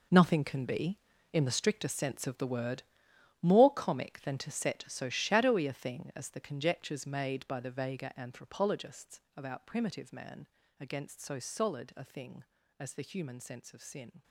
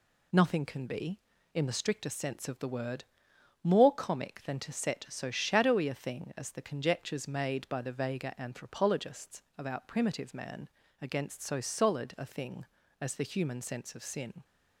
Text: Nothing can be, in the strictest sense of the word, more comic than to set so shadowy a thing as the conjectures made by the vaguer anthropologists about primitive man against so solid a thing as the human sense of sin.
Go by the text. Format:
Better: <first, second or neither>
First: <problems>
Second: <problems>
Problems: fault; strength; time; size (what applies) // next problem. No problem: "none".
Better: second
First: gets quieter; strong; throughout; 13.5 dB // pauses between "anthropologists" and "about"; slight; at 9.2 s; 0.16 s long // pauses between "man" and "against"; slight; at 10.4 s; 0.32 s long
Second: pauses between "anthropologists" and "about"; slight; at 9.4 s; 0.16 s long // pauses between "man" and "against"; slight; at 10.6 s; 0.32 s long